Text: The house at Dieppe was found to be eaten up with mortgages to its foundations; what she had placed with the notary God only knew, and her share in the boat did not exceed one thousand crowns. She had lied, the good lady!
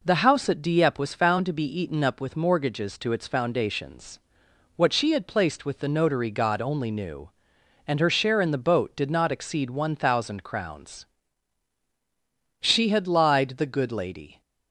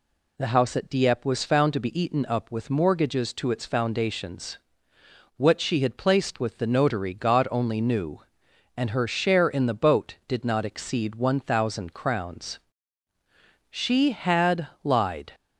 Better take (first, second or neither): first